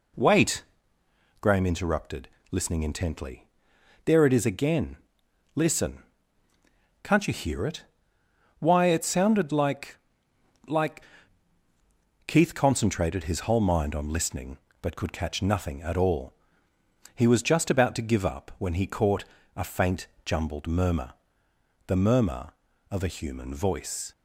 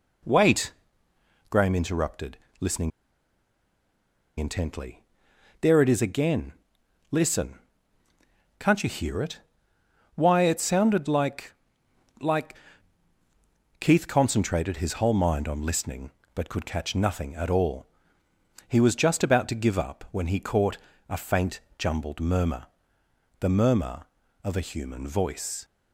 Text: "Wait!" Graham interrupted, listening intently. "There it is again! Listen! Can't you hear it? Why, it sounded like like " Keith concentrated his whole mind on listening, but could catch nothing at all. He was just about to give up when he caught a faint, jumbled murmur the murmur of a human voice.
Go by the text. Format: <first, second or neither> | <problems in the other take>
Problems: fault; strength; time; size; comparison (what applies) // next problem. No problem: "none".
first | pauses between "listening" and "intently"; strong; at 2.9 s; 1.4 s long // pauses between "like" and "like"; noticeable; at 11.5 s; 0.66 s long; noticeable in the first // pauses between "caught" and "a"; slight; at 20.7 s; 0.32 s long; slight in the first // pauses between "murmur" and "the"; noticeable; at 22.6 s; 0.72 s long; noticeable in the first